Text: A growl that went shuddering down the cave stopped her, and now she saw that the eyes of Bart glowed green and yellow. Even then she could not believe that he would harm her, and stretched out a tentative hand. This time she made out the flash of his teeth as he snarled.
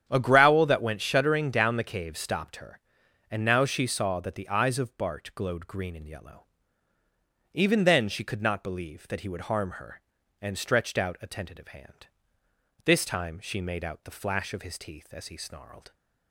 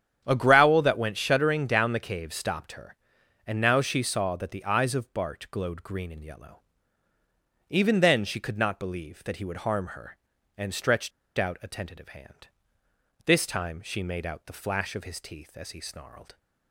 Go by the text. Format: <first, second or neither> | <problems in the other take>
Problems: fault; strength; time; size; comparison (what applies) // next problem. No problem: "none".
first | starts louder than the rest; strong; until 1.2 s; 9 dB; strong in the first // pauses between "stretched" and "out"; slight; at 11.1 s; 0.26 s long